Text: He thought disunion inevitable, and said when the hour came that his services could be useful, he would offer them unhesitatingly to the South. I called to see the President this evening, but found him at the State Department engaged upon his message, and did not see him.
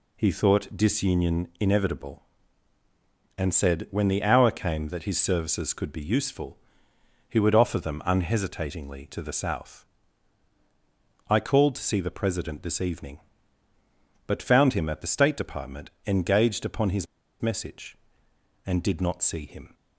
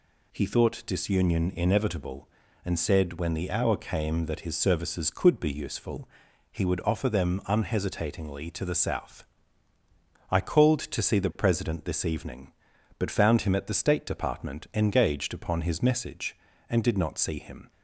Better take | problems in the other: second | pauses between "Department" and "engaged"; slight; at 15.9 s; 0.16 s long // pauses between "his" and "message"; slight; at 17.0 s; 0.35 s long

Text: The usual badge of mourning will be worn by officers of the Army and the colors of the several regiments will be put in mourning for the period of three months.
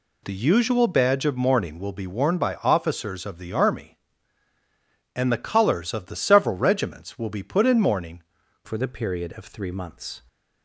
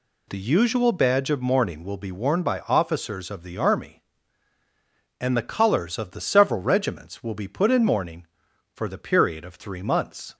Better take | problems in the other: second | changes voice at "for"; from 8.6 s on; 1.6 s long

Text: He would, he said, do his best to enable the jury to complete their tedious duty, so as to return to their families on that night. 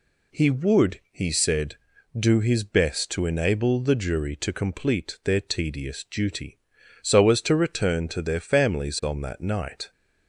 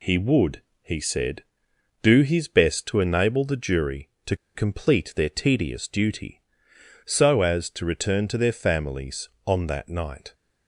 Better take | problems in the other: first | pauses between "to" and "complete"; slight; at 4.3 s; 0.20 s long

